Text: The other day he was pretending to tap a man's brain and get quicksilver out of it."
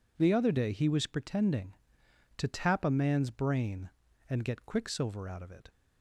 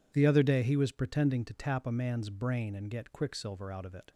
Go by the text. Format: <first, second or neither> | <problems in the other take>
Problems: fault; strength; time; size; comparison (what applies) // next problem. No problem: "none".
neither | none